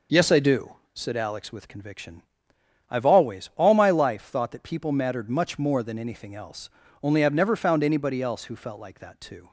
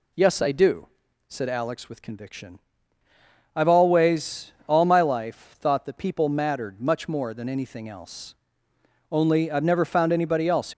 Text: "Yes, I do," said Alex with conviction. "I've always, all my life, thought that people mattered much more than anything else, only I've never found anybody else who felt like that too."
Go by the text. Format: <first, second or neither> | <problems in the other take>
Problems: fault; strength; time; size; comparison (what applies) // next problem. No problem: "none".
first | stops before "who felt like that too"; at 10.7 s